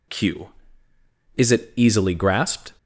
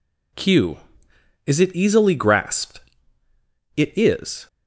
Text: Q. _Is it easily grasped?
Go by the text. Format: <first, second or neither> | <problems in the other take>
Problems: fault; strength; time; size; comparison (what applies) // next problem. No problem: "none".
first | goes on to say "It is"; noticeable; from 3.7 s on; 0.70 s long